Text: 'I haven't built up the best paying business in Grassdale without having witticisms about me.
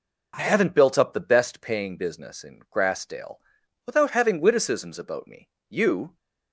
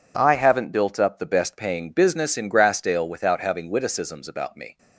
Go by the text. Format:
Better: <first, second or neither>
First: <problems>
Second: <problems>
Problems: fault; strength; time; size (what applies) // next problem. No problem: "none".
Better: second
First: pauses between "Grassdale" and "without"; noticeable; at 3.3 s; 0.50 s long // goes on to say "You"; slight; from 5.7 s on; 0.46 s long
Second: none